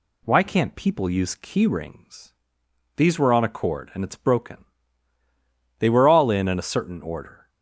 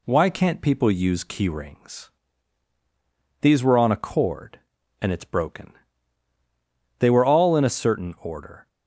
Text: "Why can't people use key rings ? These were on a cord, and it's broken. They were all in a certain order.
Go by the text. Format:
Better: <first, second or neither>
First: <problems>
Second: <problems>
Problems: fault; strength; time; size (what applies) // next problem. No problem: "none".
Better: second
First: says "in" twice; at 6.4 s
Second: none